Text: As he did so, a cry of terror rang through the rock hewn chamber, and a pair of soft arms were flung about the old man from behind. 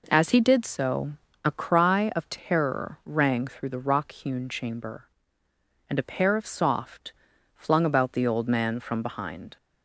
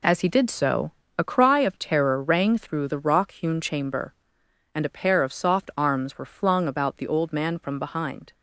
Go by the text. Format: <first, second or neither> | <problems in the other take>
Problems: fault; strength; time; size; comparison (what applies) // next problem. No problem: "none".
second | skips "arms were"; at 7.3 s